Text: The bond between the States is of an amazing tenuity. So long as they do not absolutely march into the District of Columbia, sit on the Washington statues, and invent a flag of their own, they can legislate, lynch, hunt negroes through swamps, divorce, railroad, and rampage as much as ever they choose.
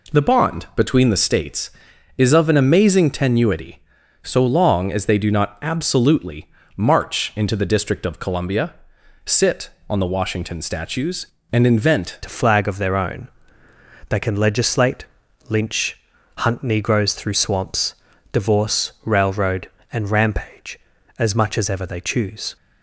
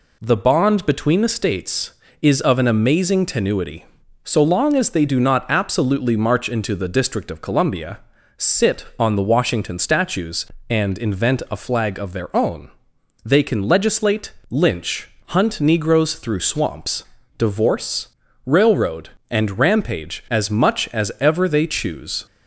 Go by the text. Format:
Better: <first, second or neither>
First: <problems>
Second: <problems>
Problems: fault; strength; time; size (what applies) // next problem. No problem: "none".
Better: second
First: pauses between "absolutely" and "march"; slight; at 6.4 s; 0.26 s long // changes voice at "a"; from 12.2 s on; 10.3 s long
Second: none